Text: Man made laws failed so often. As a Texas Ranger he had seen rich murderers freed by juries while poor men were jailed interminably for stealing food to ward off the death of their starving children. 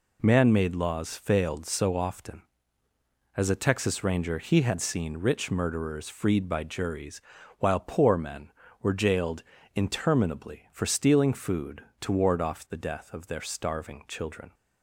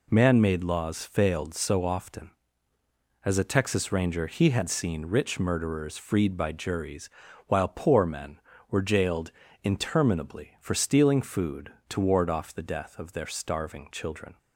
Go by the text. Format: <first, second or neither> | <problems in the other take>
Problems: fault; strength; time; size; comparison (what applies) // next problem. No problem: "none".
neither | pauses between "juries" and "while"; slight; the same in both // pauses between "jailed" and "interminably"; slight; the same in both